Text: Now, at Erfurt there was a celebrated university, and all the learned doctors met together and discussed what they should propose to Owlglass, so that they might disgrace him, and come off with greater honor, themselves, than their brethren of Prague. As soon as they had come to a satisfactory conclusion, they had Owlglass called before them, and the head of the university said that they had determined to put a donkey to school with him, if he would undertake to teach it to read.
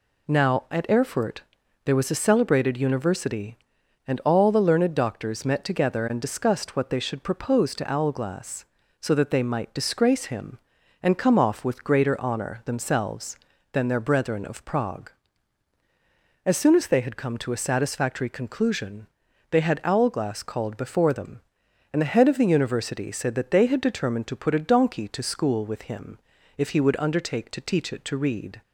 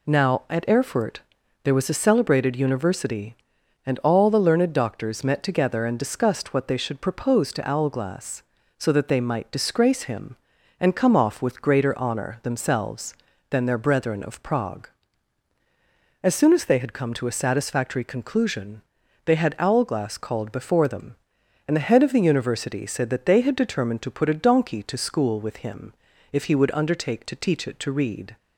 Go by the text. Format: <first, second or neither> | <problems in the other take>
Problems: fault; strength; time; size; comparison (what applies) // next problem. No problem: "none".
neither | pauses between "Erfurt" and "there"; the same in both